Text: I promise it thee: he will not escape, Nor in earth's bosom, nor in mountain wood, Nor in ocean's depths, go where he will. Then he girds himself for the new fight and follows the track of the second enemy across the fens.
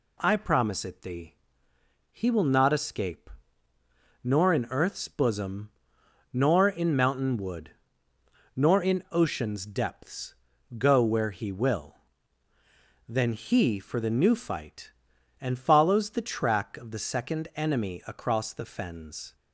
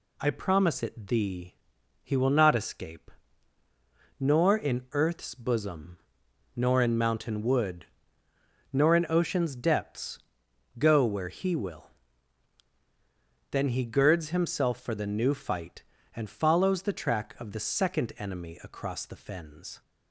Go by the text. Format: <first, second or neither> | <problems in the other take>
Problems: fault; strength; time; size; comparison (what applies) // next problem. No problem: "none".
second | skips "girds himself"; at 13.7 s